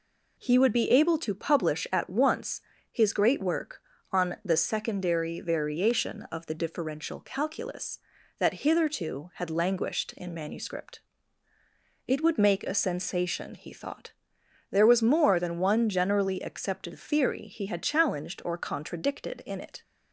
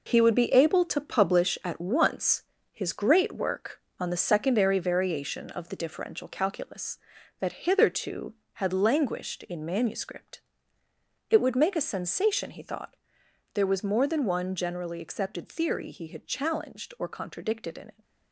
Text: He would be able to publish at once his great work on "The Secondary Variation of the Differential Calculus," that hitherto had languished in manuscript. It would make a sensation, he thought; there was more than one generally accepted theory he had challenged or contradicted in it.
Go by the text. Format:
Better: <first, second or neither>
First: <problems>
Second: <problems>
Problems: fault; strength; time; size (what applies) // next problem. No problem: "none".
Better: first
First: pauses between "once" and "his"; slight; at 2.6 s; 0.30 s long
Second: gets quieter; strong; throughout; 8 dB // pauses between "once" and "his"; slight; at 2.4 s; 0.28 s long